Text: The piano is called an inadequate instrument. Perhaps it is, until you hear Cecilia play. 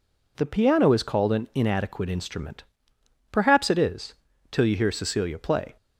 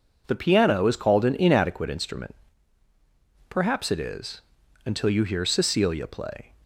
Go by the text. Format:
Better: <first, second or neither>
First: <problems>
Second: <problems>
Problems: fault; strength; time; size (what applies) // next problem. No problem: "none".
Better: second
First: says "till" for "until"; at 4.5 s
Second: none